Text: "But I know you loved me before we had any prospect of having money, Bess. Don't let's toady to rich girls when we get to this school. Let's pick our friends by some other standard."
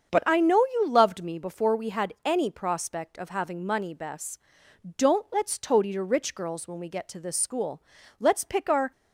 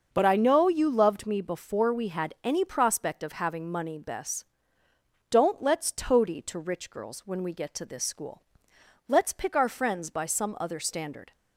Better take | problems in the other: second | starts louder than the rest; until 1.2 s; 6.5 dB; also in the second // stops before "friends by some other standard"; at 8.9 s

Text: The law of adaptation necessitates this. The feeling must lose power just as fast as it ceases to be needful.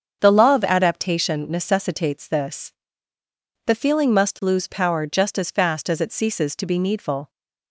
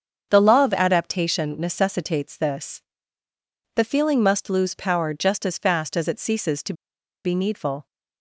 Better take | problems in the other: first | starts louder than the rest; until 1.3 s; 7 dB; also in the first // pauses between "to" and "be"; noticeable; at 6.7 s; 0.52 s long

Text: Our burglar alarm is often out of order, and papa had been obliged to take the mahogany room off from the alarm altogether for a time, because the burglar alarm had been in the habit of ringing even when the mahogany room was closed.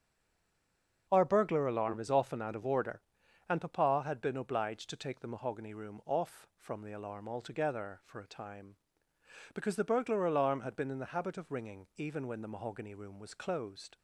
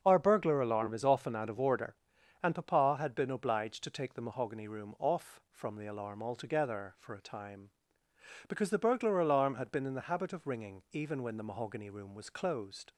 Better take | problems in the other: second | stays silent before the first word; until 1.0 s; 1.0 s long // starts louder than the rest; until 2.1 s; 6.5 dB; also in the second

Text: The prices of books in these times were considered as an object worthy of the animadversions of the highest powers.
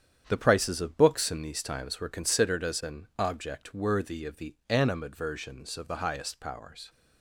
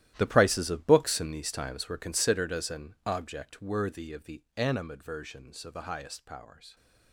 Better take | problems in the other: first | gets quieter; strong; throughout; 15.5 dB // starts louder than the rest; strong; until 1.1 s; 13.5 dB; strong in the first

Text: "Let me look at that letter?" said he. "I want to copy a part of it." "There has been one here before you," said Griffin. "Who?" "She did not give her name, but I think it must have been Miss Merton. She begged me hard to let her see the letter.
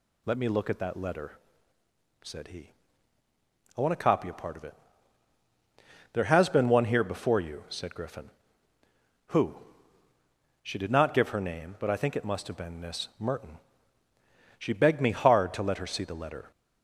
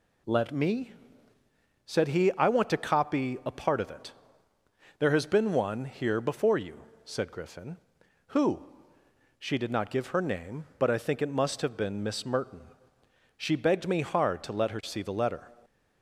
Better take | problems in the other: first | skips "look at that letter"; at 1.3 s

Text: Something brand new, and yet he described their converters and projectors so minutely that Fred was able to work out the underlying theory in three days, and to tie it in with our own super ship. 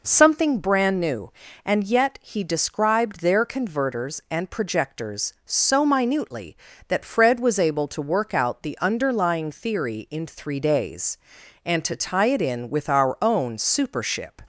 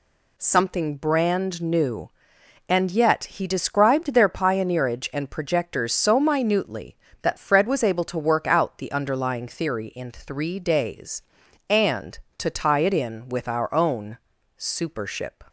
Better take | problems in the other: first | says "pioneerage" for "converters"; at 4.2 s // pauses between "own" and "super"; at 14.1 s; 0.40 s long

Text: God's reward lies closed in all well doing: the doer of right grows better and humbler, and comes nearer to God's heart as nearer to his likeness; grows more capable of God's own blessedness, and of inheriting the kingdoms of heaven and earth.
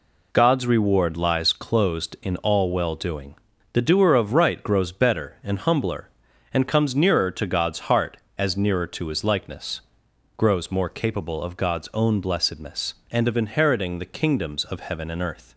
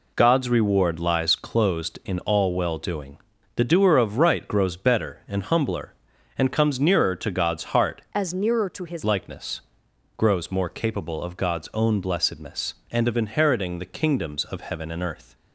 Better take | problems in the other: first | changes voice from "as" to "his"; from 8.1 to 9.0 s; 0.9 s long

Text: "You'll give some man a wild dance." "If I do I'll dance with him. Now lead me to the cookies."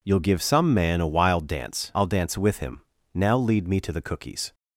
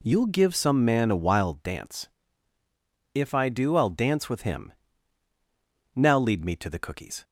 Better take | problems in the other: second | skips "If I do"; at 1.9 s

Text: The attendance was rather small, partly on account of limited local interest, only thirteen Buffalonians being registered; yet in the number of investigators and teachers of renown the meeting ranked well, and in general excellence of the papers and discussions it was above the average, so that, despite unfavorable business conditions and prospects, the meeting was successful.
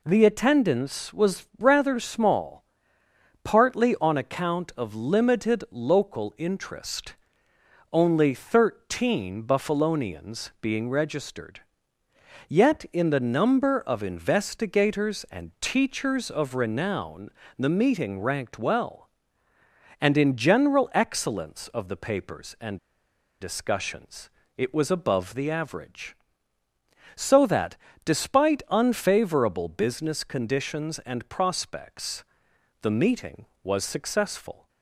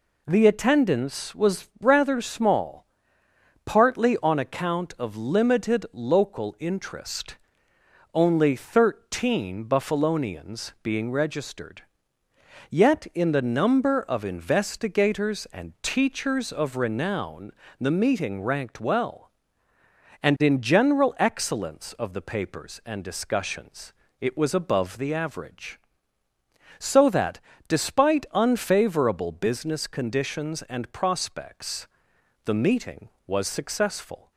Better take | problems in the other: second | pauses between "renown" and "the"; slight; at 17.3 s; 0.26 s long; slight in the second // pauses between "and" and "discussions"; noticeable; at 22.7 s; 0.64 s long // pauses between "discussions" and "it"; slight; at 24.2 s; 0.26 s long; slight in the second

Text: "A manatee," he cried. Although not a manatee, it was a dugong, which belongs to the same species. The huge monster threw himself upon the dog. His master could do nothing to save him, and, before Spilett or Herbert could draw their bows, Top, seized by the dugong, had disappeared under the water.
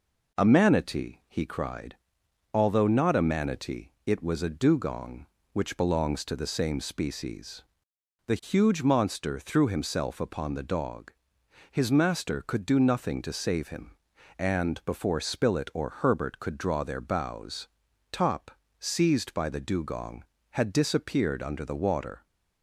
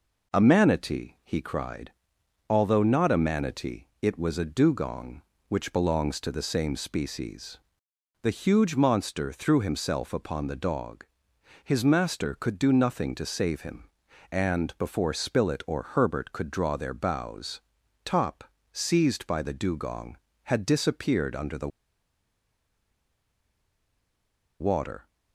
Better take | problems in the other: first | pauses between "the" and "water"; strong; at 21.6 s; 2.9 s long

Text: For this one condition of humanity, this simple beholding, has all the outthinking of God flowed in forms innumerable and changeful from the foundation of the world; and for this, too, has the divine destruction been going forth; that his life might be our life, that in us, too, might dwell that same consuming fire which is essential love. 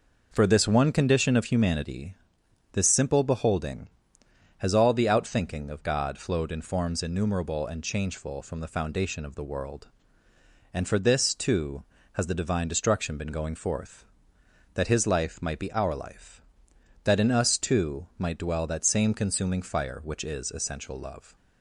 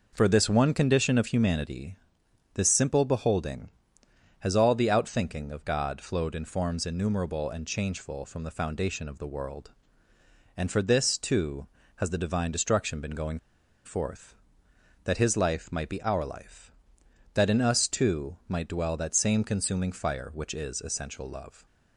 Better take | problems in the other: first | pauses between "going" and "forth"; noticeable; at 13.3 s; 0.46 s long

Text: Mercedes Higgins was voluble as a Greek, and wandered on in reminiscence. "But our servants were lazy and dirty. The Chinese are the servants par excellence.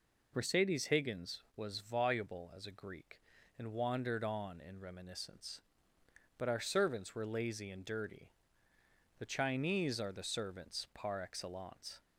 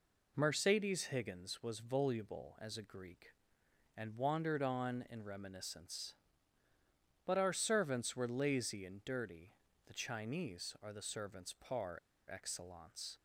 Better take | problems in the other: first | pauses between "par" and "excellence"; slight; at 11.9 s; 0.32 s long

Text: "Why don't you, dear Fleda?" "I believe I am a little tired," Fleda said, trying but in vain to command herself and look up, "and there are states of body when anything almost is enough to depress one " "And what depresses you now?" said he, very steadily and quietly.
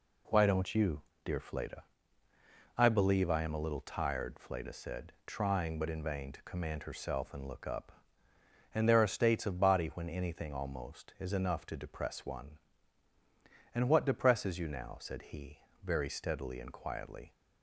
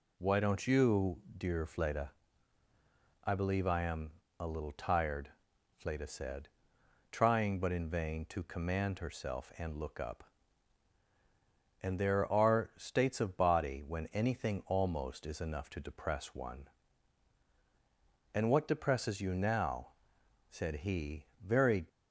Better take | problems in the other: first | pauses between "am" and "a"; slight; at 4.1 s; 0.26 s long // stops before "steadily and quietly"; at 21.8 s

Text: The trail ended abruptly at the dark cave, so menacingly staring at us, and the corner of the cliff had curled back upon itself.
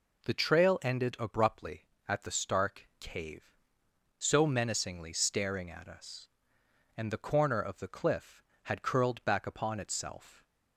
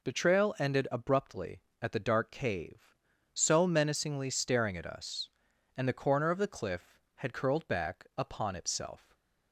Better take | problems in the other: second | says "stark" for "dark"; at 2.3 s

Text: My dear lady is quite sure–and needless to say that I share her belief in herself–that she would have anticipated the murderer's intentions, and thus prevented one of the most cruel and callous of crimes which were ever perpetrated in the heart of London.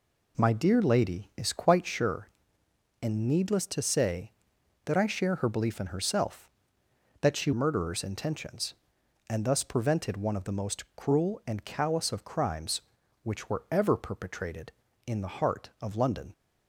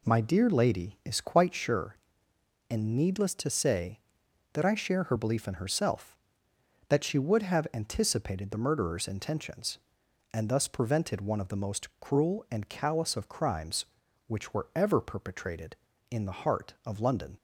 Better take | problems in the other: second | skips "would have anticipated the"; at 7.5 s

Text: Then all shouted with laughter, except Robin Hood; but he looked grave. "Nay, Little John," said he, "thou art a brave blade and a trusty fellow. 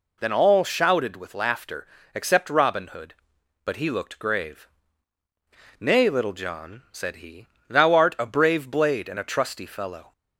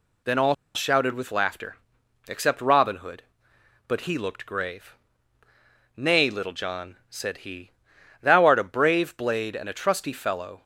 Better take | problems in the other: first | pauses between "all" and "shouted"; slight; at 0.5 s; 0.20 s long

